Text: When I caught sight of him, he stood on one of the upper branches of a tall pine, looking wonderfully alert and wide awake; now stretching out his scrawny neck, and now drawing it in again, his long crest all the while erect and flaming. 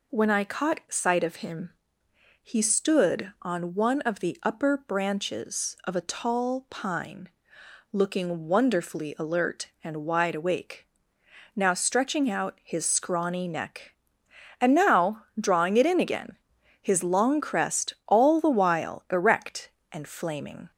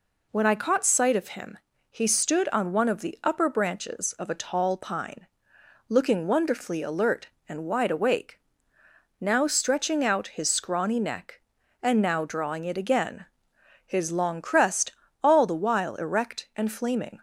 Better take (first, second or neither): first